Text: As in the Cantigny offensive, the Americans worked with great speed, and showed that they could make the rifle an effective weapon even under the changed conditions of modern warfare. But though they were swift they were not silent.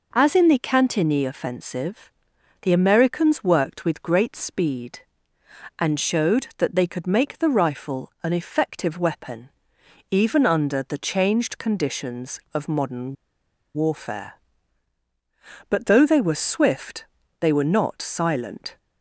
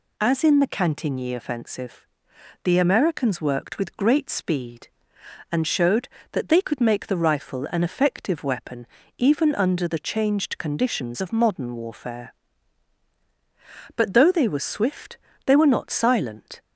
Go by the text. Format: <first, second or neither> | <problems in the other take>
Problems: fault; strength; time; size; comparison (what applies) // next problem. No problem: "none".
second | pauses between "weapon" and "even"; noticeable; at 9.4 s; 0.64 s long; slight in the second // pauses between "modern" and "warfare"; noticeable; at 13.1 s; 0.61 s long // pauses between "swift" and "they"; at 17.0 s; 0.38 s long; slight in the second